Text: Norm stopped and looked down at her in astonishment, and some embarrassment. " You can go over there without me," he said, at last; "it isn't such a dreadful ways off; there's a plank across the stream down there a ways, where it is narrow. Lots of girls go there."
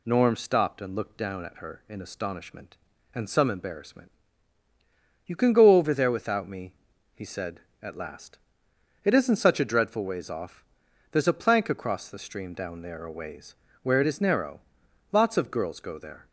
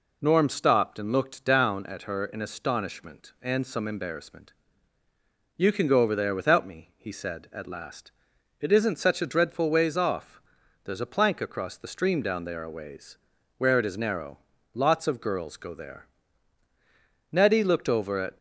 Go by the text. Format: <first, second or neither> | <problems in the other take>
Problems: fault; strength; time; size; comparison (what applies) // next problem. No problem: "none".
first | goes on to say "Nettie looked over at"; noticeable; from 17.3 s on; 1.0 s long